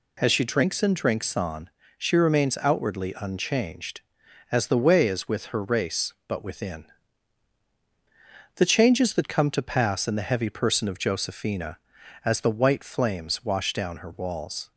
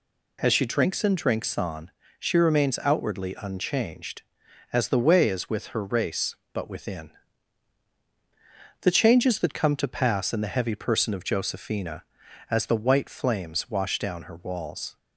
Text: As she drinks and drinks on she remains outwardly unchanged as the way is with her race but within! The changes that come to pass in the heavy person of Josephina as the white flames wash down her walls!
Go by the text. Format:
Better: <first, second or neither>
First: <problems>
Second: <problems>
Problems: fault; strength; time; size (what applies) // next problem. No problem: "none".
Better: neither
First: pauses between "on" and "she"; slight; at 1.7 s; 0.26 s long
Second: pauses between "on" and "she"; slight; at 1.9 s; 0.26 s long